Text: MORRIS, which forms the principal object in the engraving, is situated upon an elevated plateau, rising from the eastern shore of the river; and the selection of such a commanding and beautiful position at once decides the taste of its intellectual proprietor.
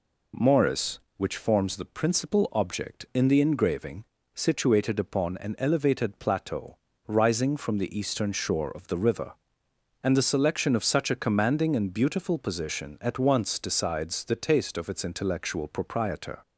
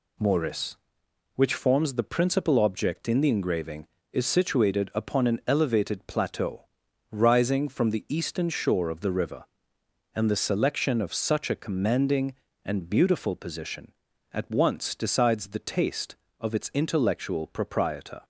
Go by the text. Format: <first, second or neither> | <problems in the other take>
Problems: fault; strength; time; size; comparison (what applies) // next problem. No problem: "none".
second | skips "is"; at 4.1 s